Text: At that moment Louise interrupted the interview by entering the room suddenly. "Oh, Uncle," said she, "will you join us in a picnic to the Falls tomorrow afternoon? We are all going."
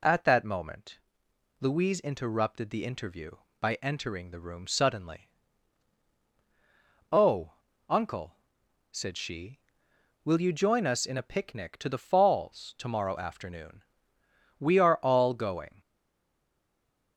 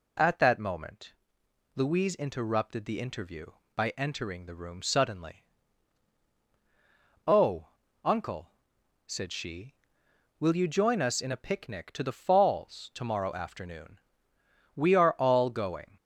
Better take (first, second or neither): second